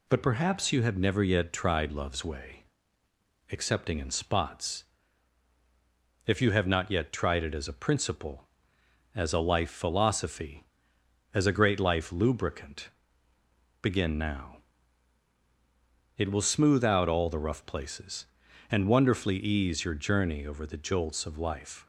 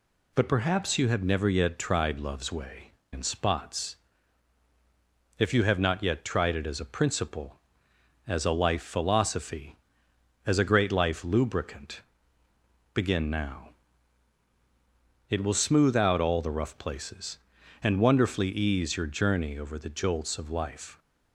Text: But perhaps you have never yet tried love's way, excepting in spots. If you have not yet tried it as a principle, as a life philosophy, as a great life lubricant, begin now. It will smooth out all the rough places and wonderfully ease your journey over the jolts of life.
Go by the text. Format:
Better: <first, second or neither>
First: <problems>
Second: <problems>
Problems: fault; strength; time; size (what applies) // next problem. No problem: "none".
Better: first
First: none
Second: skips "excepting"; at 3.0 s